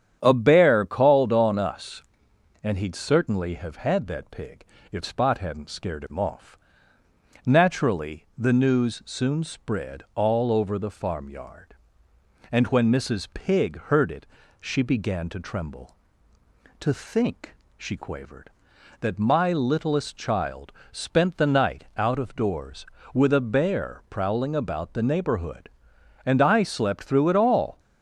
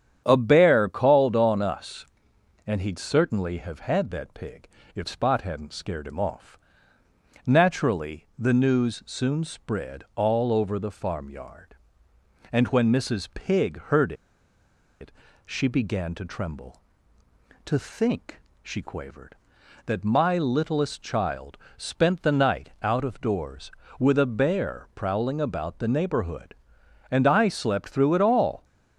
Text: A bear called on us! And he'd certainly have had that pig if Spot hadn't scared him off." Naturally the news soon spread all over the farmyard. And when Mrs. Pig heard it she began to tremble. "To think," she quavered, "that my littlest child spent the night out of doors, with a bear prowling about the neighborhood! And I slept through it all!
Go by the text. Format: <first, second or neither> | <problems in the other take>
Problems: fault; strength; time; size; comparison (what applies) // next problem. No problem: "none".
first | starts louder than the rest; strong; until 1.2 s; 9 dB; strong in the first // pauses between "pig" and "if"; slight; at 4.6 s; 0.28 s long; slight in the first // pauses between "heard" and "it"; noticeable; at 14.1 s; 0.87 s long // pauses between "it" and "she"; slight; at 15.1 s; 0.36 s long; slight in the first // pauses between "child" and "spent"; slight; at 21.5 s; 0.22 s long; slight in the first